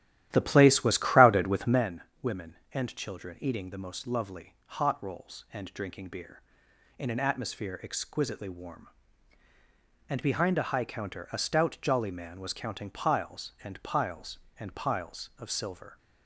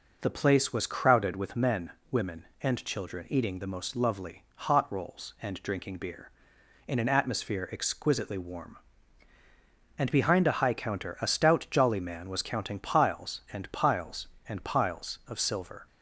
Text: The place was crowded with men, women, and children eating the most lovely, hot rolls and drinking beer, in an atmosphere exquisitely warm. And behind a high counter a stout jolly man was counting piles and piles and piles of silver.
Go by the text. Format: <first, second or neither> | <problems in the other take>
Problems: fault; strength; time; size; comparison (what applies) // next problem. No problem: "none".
second | starts louder than the rest; strong; until 1.9 s; 13 dB